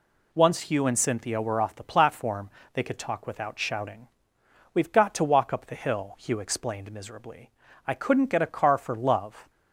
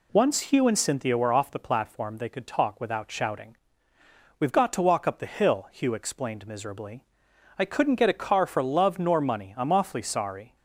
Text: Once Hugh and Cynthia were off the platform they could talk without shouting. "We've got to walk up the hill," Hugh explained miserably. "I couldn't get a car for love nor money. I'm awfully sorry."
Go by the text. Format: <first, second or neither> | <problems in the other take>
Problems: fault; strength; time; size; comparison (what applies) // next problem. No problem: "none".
second | pauses between "platform" and "they"; slight; at 2.4 s; 0.24 s long // stops before "nor money I'm awfully sorry"; at 9.4 s